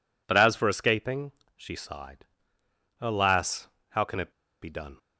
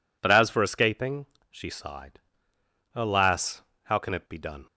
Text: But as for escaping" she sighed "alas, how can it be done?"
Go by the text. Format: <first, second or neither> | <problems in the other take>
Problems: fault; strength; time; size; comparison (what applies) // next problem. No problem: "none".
second | pauses between "escaping" and "she"; slight; at 1.3 s; 0.22 s long; slight in the second // pauses between "sighed" and "alas"; noticeable; at 2.2 s; 0.74 s long; noticeable in the second // pauses between "it" and "be"; slight; at 4.3 s; 0.31 s long